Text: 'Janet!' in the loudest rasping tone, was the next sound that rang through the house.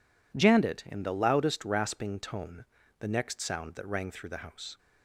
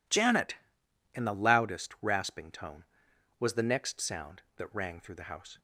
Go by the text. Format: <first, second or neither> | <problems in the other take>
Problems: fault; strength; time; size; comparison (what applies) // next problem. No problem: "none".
second | skips "was"; at 2.8 s